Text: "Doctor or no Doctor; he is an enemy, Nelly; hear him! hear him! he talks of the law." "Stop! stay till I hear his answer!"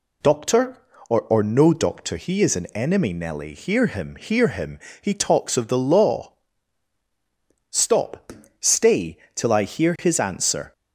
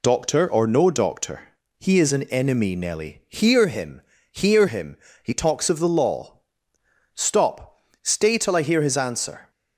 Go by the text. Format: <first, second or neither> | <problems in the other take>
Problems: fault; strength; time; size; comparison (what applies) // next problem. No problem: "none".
second | says "or" twice; at 1.2 s // pauses between "stay" and "till"; slight; at 9.1 s; 0.16 s long